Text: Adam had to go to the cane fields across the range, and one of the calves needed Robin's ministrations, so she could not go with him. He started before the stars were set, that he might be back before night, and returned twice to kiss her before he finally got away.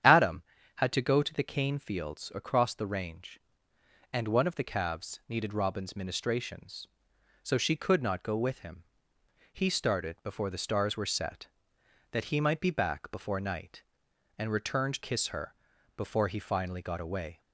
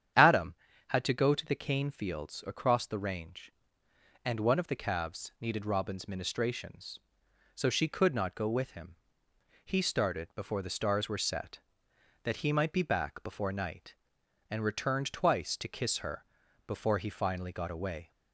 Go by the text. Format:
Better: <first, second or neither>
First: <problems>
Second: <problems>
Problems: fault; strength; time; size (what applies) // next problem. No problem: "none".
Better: second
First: starts louder than the rest; strong; until 1.3 s; 9.5 dB // skips "twice to"; at 15.0 s // pauses between "her" and "before"; at 15.5 s; 0.42 s long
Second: starts louder than the rest; strong; until 1.5 s; 9.5 dB // pauses between "her" and "before"; at 16.2 s; 0.42 s long